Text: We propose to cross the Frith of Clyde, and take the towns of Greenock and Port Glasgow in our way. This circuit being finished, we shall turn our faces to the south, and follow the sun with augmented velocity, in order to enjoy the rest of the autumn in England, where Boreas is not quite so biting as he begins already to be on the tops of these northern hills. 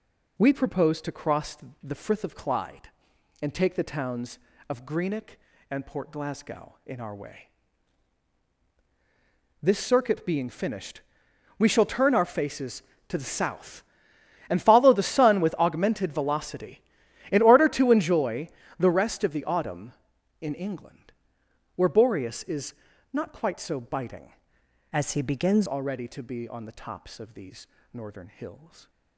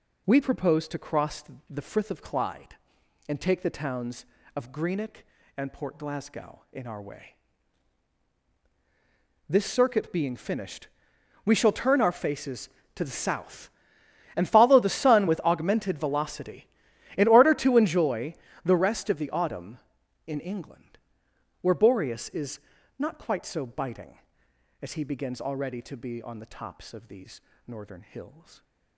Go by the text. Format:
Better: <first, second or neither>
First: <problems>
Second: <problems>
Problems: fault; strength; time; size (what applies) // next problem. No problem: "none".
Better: second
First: pauses between "cross" and "the"; slight; at 1.5 s; 0.24 s long // pauses between "enjoy" and "the"; slight; at 18.4 s; 0.30 s long // pauses between "is" and "not"; at 22.7 s; 0.38 s long // changes voice from "as" to "begins"; from 24.9 to 25.6 s; 0.7 s long // pauses between "these" and "northern"; slight; at 27.6 s; 0.26 s long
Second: pauses between "cross" and "the"; slight; at 1.4 s; 0.24 s long // pauses between "enjoy" and "the"; slight; at 18.3 s; 0.30 s long // pauses between "is" and "not"; at 22.5 s; 0.38 s long // pauses between "these" and "northern"; slight; at 27.4 s; 0.26 s long